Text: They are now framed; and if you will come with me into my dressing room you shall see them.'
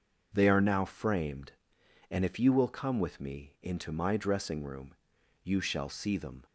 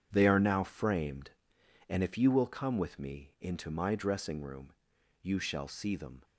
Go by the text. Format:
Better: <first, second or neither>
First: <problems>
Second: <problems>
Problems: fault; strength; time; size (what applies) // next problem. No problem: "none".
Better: first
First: pauses between "room" and "you"; noticeable; at 4.9 s; 0.48 s long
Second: gets quieter; strong; throughout; 11 dB // pauses between "room" and "you"; noticeable; at 4.7 s; 0.48 s long